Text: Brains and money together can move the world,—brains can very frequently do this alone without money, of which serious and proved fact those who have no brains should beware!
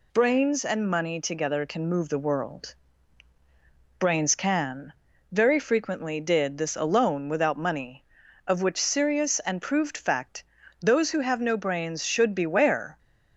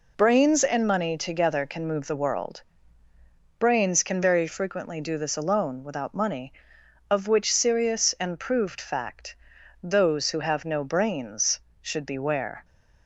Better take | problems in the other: second | pauses between "can" and "very"; at 4.9 s; 0.38 s long // says "did" for "do"; at 6.2 s // pauses between "fact" and "those"; at 10.4 s; 0.38 s long; noticeable in the second

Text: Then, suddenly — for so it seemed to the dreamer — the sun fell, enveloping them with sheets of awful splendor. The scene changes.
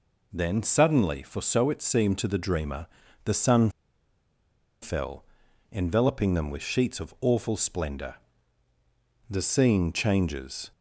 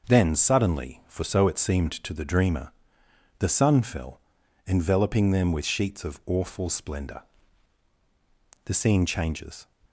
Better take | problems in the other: second | pauses between "sun" and "fell"; at 3.6 s; 1.1 s long

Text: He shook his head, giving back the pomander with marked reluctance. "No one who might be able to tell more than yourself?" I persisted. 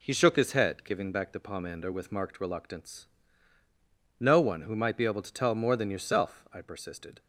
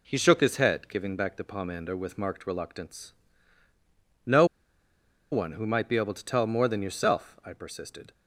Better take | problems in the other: first | pauses between "No" and "one"; noticeable; at 4.4 s; 0.86 s long

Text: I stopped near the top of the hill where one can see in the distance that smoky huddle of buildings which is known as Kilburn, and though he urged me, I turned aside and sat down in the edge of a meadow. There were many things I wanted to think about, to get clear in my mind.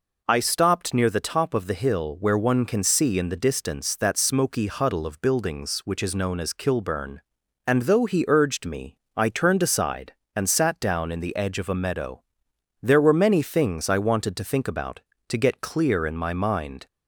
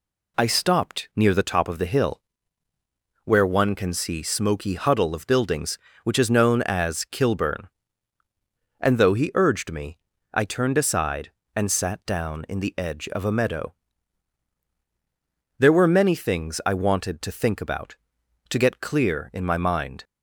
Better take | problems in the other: first | pauses between "hill" and "where"; at 2.1 s; 1.0 s long // skips "in the distance that"; at 4.2 s

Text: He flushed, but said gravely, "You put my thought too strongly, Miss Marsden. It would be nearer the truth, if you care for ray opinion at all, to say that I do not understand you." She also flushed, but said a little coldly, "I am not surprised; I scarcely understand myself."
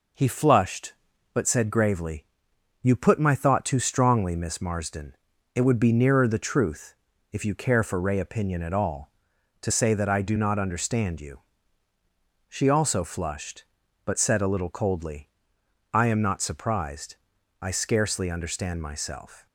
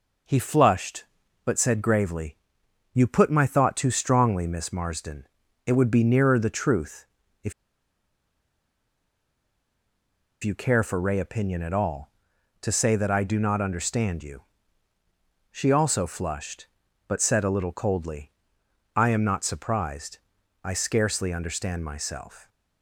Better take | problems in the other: first | pauses between "if" and "you"; strong; at 7.5 s; 2.9 s long

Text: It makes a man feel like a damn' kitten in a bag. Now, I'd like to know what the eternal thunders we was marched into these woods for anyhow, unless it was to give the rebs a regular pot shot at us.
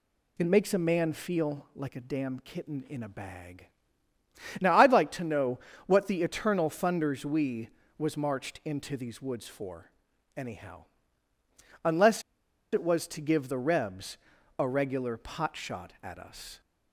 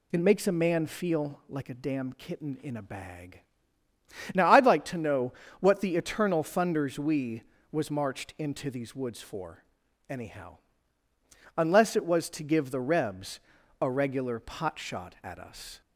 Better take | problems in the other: second | pauses between "know" and "what"; slight; at 5.5 s; 0.30 s long; slight in the second // pauses between "for" and "anyhow"; noticeable; at 9.8 s; 0.46 s long; noticeable in the second // pauses between "unless" and "it"; noticeable; at 12.2 s; 0.50 s long // pauses between "rebs" and "a"; at 14.1 s; 0.42 s long; also in the second

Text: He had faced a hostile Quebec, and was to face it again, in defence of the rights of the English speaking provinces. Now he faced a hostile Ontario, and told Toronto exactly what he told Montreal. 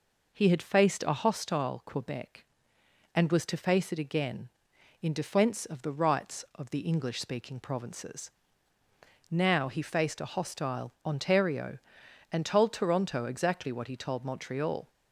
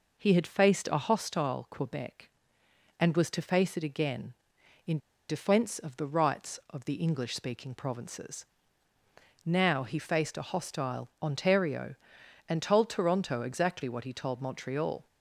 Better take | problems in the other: first | pauses between "in" and "defence"; slight; at 4.9 s; 0.31 s long

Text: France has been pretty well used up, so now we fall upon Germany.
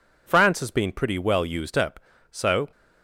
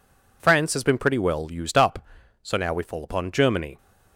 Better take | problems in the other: second | stops before "now we fall upon Germany"; at 2.7 s

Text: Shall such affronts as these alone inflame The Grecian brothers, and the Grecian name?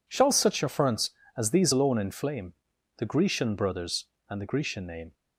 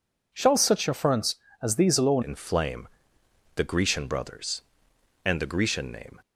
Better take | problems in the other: first | changes voice at "inflame"; from 2.2 s on; 3.9 s long // pauses between "inflame" and "The"; noticeable; at 2.8 s; 0.66 s long; also in the first

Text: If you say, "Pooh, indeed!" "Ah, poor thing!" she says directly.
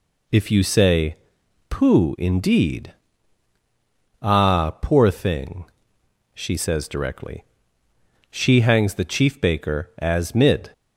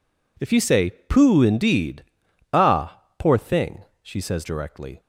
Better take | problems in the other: second | goes on to say "She hangs the chief baker as mid"; strong; from 8.3 s on; 2.4 s long

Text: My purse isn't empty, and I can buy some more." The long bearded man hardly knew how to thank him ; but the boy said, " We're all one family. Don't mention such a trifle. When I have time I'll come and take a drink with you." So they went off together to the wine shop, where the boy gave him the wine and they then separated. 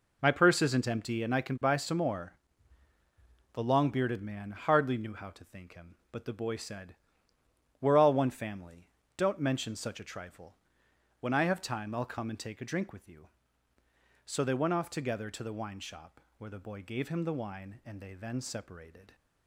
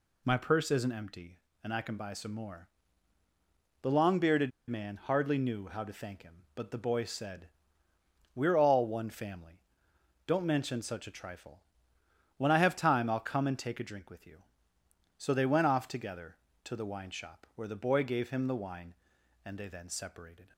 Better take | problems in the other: first | pauses between "bearded" and "man"; slight; at 4.5 s; 0.19 s long

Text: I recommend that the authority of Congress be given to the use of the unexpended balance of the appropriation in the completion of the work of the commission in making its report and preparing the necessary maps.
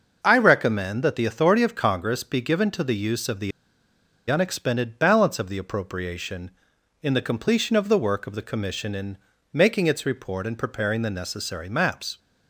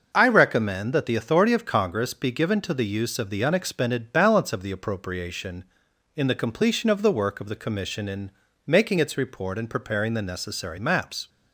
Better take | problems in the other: second | starts louder than the rest; noticeable; until 1.2 s; 6 dB; noticeable in the second // pauses between "the" and "unexpended"; noticeable; at 3.5 s; 0.79 s long // pauses between "in" and "making"; slight; at 9.1 s; 0.36 s long; slight in the second

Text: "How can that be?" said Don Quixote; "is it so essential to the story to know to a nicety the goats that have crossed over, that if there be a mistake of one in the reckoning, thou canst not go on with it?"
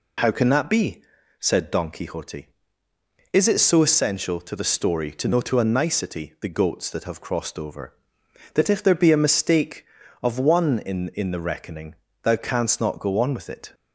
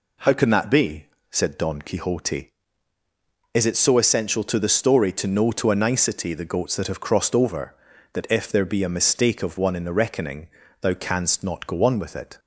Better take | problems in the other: second | says "in" twice; at 11.1 s

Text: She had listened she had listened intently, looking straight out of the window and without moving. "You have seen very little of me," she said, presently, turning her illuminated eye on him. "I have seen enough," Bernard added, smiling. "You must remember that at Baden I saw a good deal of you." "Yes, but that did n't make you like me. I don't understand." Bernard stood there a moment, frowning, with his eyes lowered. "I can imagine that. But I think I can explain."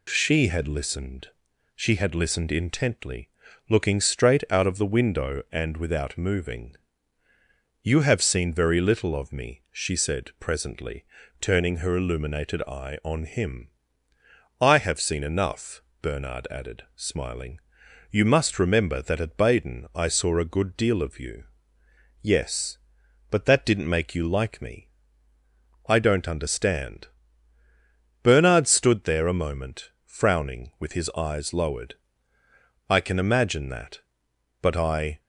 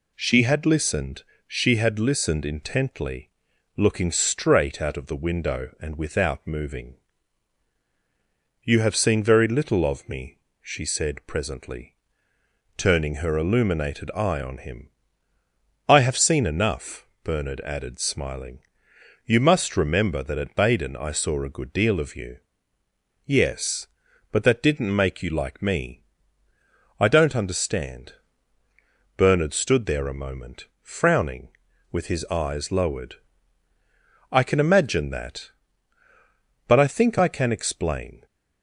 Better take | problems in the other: second | pauses between "listened" and "she"; noticeable; at 1.2 s; 0.48 s long; slight in the second // stops before "think I can explain"; at 35.2 s

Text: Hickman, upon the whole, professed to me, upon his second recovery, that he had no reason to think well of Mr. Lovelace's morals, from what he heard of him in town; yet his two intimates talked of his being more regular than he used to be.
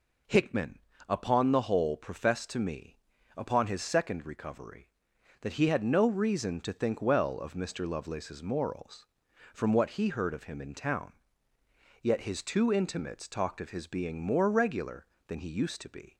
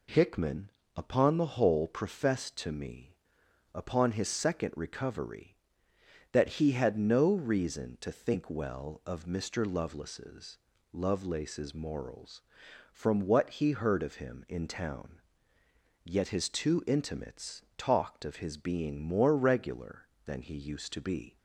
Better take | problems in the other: first | says "Lovelace's" twice; at 10.9 s // pauses between "intimates" and "talked"; slight; at 17.6 s; 0.16 s long

